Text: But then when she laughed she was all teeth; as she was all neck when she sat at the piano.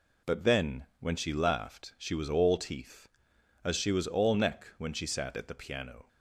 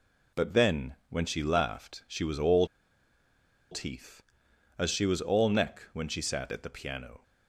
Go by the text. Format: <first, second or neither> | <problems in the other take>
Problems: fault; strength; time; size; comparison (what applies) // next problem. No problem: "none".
first | pauses between "all" and "teeth"; at 2.6 s; 1.0 s long